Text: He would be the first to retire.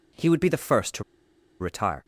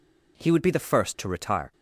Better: second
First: pauses between "to" and "retire"; noticeable; at 1.0 s; 0.57 s long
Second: none

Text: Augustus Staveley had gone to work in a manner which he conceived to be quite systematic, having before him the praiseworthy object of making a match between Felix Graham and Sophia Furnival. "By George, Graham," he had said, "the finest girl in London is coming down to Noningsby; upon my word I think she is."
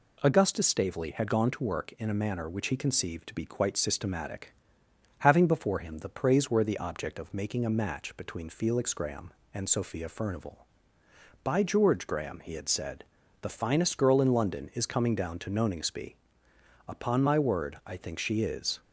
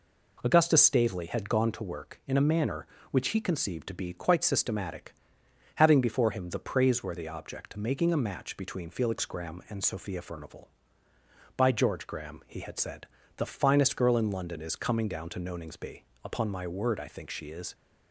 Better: first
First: none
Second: skips "of"; at 7.7 s

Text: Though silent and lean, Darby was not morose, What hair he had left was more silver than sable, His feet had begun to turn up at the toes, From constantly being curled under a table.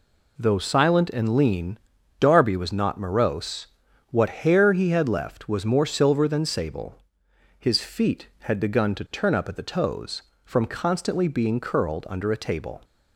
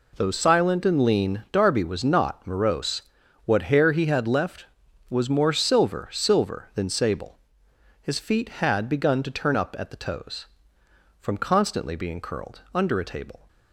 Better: first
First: none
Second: says "silver" twice; at 6.1 s

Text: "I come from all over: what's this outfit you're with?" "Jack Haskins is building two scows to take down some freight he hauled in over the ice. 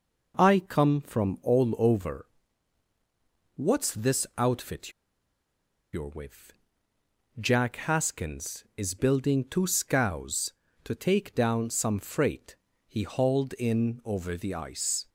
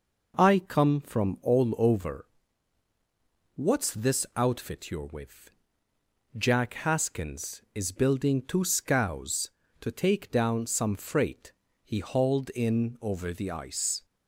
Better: second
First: pauses between "outfit" and "you're"; at 4.9 s; 1.0 s long // pauses between "freight" and "he"; slight; at 12.5 s; 0.32 s long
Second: pauses between "freight" and "he"; slight; at 11.5 s; 0.32 s long

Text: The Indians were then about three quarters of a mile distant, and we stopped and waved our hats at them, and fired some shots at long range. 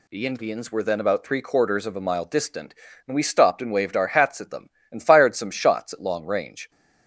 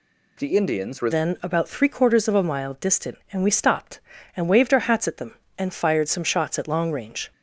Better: first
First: none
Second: changes voice at "then"; from 1.1 s on; 6.2 s long

